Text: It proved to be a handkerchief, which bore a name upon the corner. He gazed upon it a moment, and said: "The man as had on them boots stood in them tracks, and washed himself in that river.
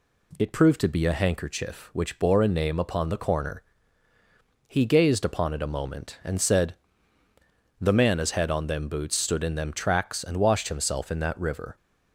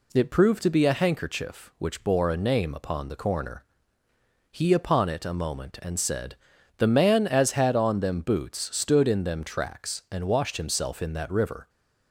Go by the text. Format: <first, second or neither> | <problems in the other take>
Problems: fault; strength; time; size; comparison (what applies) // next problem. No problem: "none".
first | skips "gazed"; at 4.7 s